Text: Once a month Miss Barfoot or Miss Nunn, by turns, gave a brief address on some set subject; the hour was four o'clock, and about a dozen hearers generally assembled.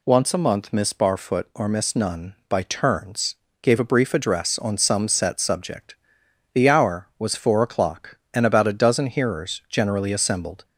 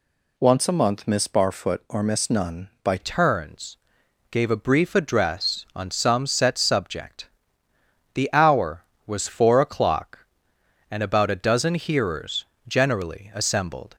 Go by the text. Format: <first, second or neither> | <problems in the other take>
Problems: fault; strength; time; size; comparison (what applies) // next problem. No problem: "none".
first | changes voice at "turns"; from 2.9 s on; 11.0 s long // pauses between "hearers" and "generally"; slight; at 12.4 s; 0.20 s long